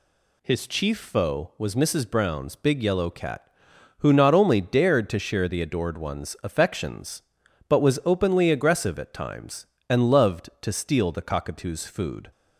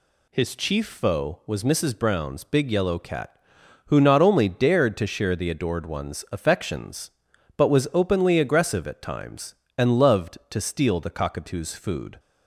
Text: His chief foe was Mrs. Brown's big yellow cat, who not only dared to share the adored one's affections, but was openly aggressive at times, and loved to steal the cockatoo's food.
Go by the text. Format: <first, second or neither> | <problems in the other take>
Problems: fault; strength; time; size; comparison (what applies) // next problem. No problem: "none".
neither | none